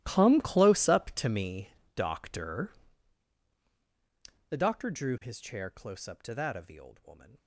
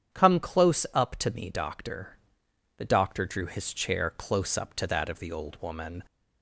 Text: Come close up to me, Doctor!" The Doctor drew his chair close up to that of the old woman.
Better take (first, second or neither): second